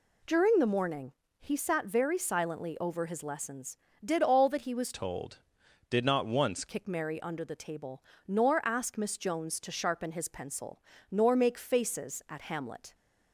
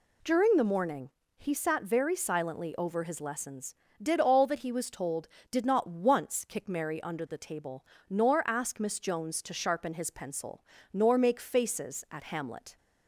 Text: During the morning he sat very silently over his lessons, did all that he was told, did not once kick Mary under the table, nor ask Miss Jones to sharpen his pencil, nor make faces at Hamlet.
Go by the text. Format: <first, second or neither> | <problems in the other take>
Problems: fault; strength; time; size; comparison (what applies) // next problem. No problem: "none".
second | pauses between "morning" and "he"; slight; at 1.1 s; 0.28 s long; slight in the second // changes voice from "told" to "once"; from 4.9 to 6.6 s; 1.7 s long